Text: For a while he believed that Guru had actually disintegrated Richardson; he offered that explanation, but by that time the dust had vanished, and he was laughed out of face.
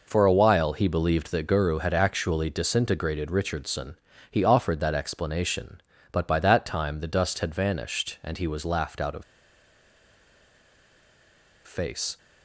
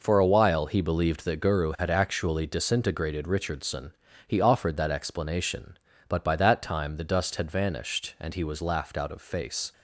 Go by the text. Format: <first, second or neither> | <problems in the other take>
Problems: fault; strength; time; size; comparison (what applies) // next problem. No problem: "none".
second | pauses between "of" and "face"; strong; at 9.2 s; 2.4 s long